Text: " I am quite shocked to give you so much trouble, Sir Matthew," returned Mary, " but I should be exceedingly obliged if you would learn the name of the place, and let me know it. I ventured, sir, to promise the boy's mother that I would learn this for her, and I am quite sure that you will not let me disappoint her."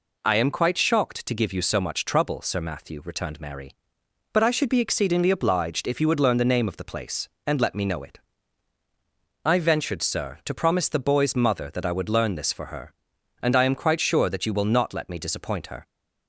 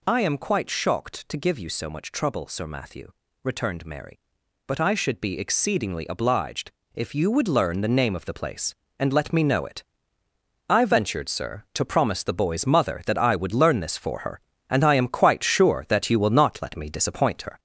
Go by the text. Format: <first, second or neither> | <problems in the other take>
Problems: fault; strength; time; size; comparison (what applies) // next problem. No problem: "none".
first | gets louder; strong; throughout; 7.5 dB // pauses between "obliged" and "if"; slight; at 6.7 s; 0.22 s long